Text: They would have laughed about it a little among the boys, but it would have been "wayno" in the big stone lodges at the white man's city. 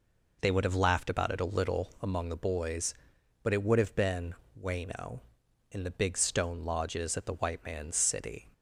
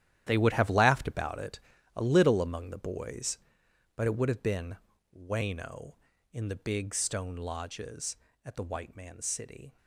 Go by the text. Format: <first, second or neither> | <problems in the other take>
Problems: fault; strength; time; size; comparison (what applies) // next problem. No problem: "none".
first | gets quieter; strong; throughout; 13.5 dB // pauses between "it" and "a"; at 1.5 s; 0.38 s long // pauses between "been" and "wayno"; at 4.7 s; 0.42 s long; slight in the first